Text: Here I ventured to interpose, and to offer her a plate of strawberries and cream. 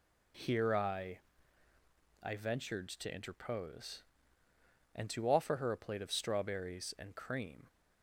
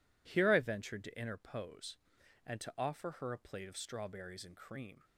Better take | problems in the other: second | says "I" twice; at 2.2 s

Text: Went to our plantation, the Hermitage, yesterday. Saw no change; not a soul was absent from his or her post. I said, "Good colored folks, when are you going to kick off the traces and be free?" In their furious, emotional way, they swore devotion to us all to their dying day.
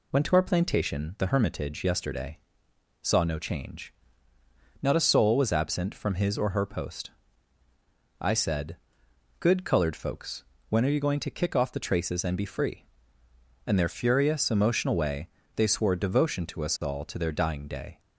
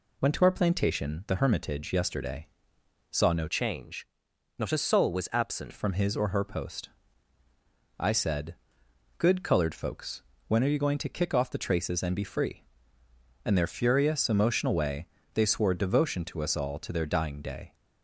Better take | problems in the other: first | changes voice from "change" to "absent"; from 3.4 to 5.7 s; 2.3 s long

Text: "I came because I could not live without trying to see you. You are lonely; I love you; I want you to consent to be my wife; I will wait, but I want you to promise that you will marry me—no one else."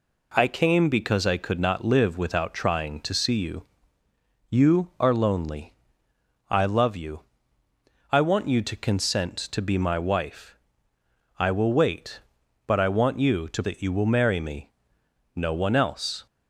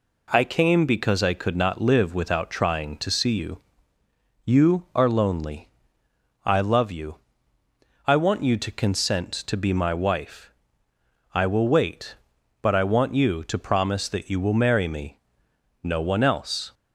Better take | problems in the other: second | skips "promise"; at 13.6 s

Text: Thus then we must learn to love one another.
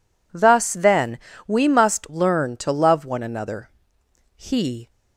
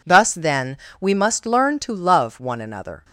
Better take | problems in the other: second | pauses between "then" and "we"; slight; at 1.1 s; 0.30 s long; slight in the second // goes on to say "He"; from 4.3 s on; 0.54 s long

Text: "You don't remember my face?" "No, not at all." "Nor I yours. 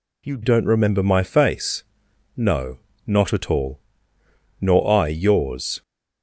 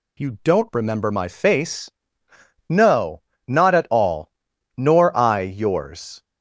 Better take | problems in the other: second | changes voice at "don't"; from 0.4 s on; 5.4 s long

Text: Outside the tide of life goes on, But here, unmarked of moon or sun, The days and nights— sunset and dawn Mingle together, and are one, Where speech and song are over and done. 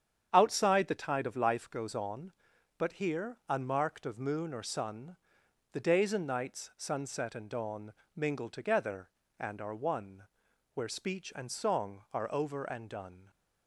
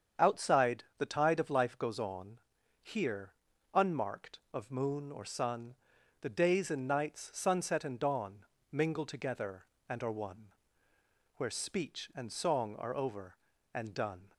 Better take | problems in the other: first | starts louder than the rest; strong; until 1.3 s; 7.5 dB; strong in the first // skips "But"; at 2.5 s // pauses between "dawn" and "Mingle"; slight; at 8.4 s; 0.26 s long; slight in the first

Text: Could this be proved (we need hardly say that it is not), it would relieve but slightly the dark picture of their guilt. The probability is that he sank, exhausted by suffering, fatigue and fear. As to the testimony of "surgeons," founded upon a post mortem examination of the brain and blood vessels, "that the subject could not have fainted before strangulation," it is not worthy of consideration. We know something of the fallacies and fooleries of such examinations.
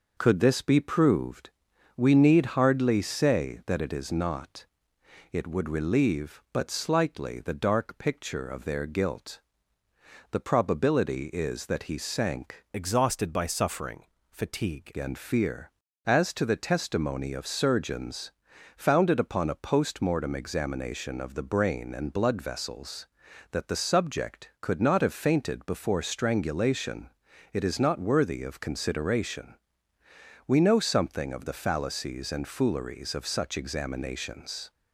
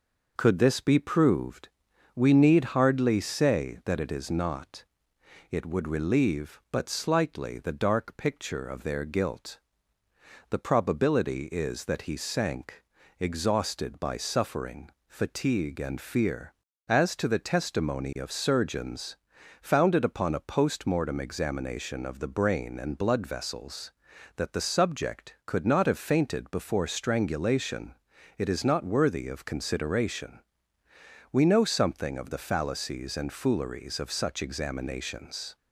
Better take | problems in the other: second | changes voice from "exhausted" to "fatigue"; from 12.7 to 14.9 s; 2.2 s long

